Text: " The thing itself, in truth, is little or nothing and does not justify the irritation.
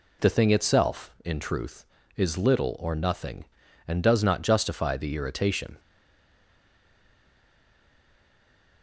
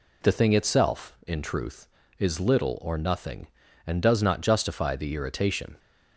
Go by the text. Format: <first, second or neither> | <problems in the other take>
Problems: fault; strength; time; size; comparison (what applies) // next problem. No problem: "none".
second | stays silent after the last word; strong; from 5.7 s on; 3.1 s long